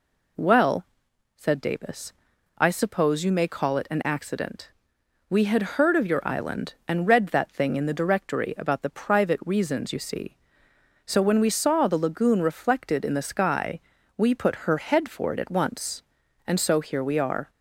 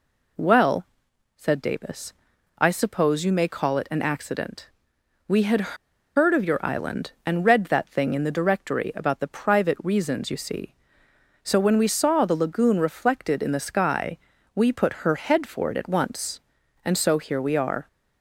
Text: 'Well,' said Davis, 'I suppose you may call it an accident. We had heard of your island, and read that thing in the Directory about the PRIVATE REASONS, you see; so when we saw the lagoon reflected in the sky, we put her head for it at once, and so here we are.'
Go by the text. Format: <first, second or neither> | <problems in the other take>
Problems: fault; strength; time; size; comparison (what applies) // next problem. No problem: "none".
first | pauses between "had" and "heard"; at 5.7 s; 0.40 s long